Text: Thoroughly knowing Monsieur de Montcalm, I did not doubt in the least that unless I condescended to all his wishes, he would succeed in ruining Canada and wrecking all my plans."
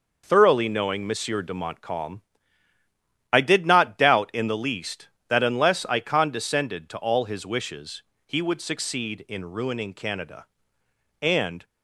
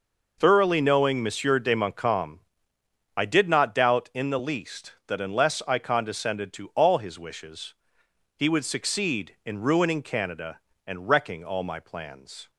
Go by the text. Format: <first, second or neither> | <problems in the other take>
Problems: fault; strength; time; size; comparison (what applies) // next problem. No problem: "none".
second | stops before "wrecking all my plans"; at 11.6 s